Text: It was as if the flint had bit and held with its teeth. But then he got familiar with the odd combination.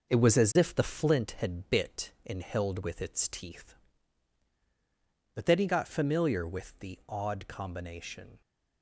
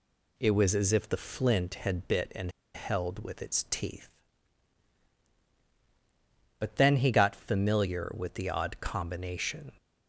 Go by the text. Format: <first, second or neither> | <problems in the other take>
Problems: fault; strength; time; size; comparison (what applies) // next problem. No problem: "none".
first | pauses between "and" and "held"; slight; at 2.5 s; 0.24 s long